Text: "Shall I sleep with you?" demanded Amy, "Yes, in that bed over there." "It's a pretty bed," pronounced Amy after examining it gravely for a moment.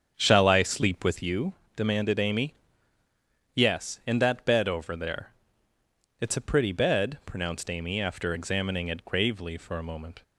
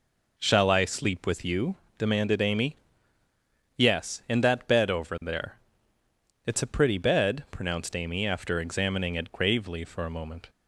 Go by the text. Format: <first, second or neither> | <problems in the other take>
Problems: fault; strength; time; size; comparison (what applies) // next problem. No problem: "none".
second | starts louder than the rest; strong; until 1.2 s; 7.5 dB